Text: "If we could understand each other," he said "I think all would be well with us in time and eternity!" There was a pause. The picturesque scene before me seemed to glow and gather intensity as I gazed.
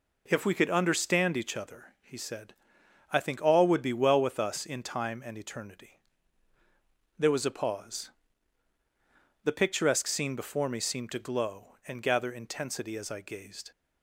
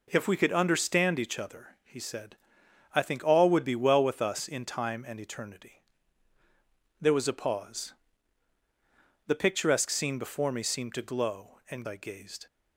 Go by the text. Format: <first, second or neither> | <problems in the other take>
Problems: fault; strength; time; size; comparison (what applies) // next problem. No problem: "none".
first | pauses between "said" and "I"; noticeable; at 2.3 s; 0.60 s long; noticeable in the first // skips "gather intensity as"; at 11.8 s